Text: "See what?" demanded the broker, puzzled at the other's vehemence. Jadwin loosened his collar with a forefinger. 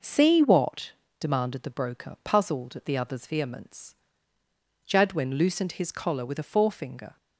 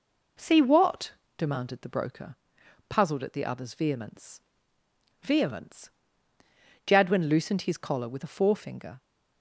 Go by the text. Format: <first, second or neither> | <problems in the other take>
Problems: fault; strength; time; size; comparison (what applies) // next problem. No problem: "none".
first | says "vehemence" twice; at 5.1 s